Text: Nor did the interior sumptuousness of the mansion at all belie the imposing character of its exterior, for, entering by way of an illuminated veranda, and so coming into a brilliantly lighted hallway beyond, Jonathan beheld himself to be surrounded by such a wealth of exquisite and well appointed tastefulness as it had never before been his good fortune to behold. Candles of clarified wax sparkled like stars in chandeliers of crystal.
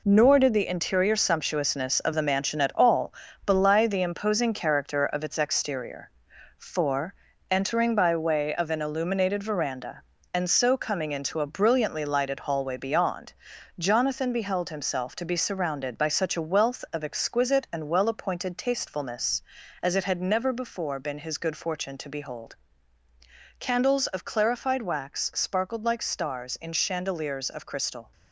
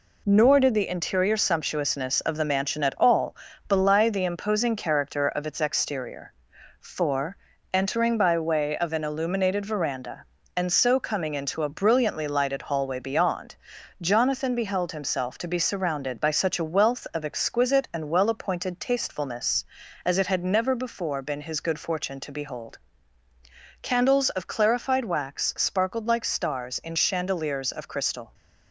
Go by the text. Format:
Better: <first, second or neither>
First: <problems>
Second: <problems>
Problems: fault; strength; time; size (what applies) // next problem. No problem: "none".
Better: second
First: gets quieter; strong; throughout; 8 dB // pauses between "all" and "belie"; slight; at 3.1 s; 0.32 s long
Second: pauses between "all" and "belie"; slight; at 3.3 s; 0.32 s long